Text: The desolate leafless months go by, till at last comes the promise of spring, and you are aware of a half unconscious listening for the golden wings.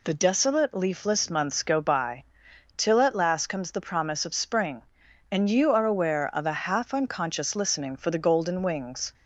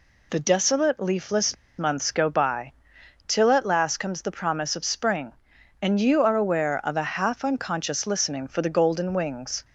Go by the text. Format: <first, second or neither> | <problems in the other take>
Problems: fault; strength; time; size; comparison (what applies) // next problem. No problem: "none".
first | pauses between "leafless" and "months"; slight; at 1.5 s; 0.23 s long